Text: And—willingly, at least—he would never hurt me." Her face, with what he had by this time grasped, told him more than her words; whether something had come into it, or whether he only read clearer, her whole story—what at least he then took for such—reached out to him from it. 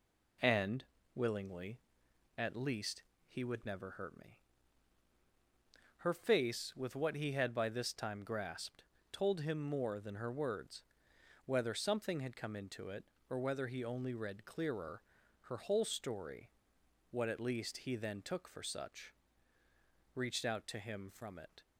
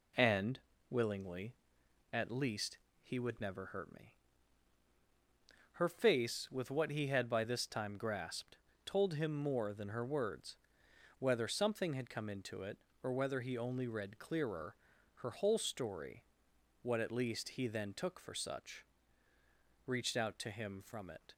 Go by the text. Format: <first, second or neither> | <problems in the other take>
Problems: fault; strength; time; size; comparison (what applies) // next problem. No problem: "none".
neither | none